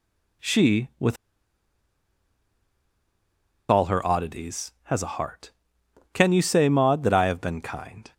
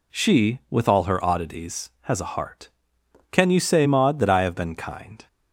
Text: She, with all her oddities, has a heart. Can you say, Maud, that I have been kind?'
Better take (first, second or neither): second